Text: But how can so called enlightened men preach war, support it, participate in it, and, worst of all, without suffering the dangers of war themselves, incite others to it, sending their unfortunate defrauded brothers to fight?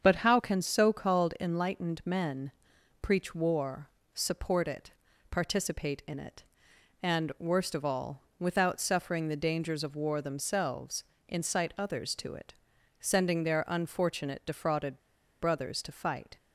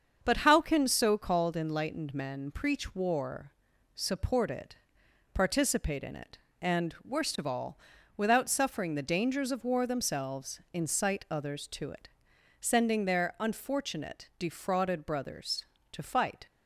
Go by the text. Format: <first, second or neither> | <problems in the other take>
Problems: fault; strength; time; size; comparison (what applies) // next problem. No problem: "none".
second | starts louder than the rest; strong; until 1.0 s; 7 dB; also in the second // pauses between "men" and "preach"; noticeable; at 2.5 s; 0.50 s long // pauses between "defrauded" and "brothers"; at 14.9 s; 0.42 s long